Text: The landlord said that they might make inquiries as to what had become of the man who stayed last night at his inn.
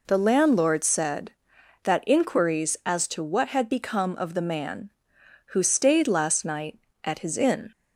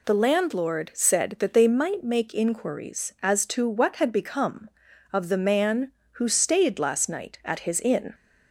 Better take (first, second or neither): second